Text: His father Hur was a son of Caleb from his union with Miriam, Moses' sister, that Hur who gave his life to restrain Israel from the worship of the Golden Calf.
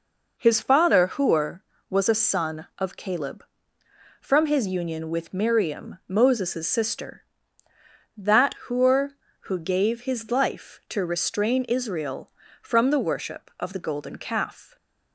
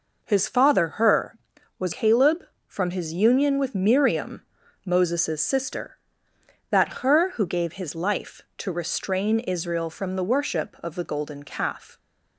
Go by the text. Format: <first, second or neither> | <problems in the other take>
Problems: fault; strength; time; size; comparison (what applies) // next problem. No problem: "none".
first | skips "a son of"; at 1.9 s